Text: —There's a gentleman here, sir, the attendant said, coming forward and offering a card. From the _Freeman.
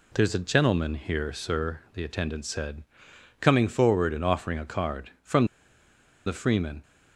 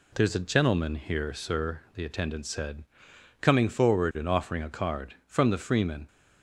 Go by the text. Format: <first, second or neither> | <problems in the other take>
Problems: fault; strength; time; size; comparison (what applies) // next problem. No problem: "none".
second | pauses between "From" and "the"; noticeable; at 5.4 s; 0.79 s long